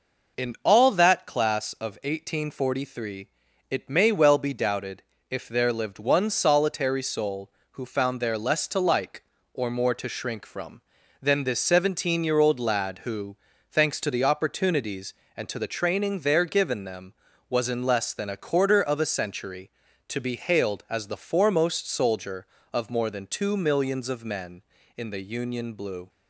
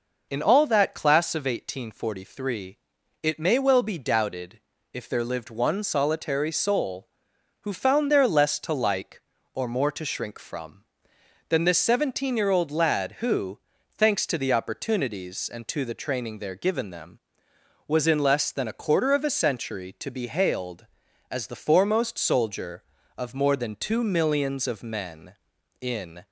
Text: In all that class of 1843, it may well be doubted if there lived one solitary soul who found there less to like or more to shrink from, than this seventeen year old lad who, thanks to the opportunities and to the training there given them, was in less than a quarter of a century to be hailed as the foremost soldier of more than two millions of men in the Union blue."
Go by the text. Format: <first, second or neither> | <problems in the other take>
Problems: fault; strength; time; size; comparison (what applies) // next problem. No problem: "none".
first | pauses between "doubted" and "if"; slight; at 4.6 s; 0.32 s long; slight in the first // stops before "the Union blue"; at 26.2 s